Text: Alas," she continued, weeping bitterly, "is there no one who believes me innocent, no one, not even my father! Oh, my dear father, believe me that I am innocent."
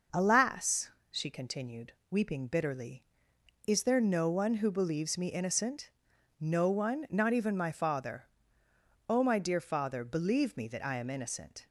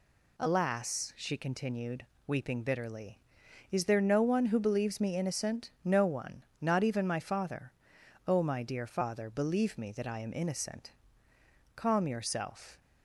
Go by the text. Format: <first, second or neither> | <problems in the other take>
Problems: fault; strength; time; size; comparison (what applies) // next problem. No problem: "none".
first | goes on to say "Calm yourself"; noticeable; from 11.7 s on; 1.0 s long